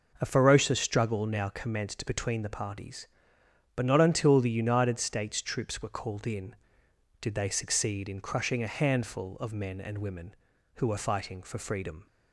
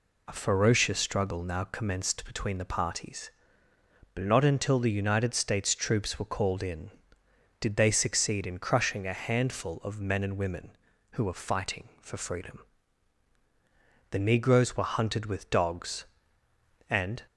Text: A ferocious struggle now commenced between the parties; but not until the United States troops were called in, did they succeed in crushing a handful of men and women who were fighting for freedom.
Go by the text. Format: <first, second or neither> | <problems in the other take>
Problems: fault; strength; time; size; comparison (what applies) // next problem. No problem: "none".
first | goes on to say "The negroes were hunted with dogs and"; strong; from 14.1 s on; 3.1 s long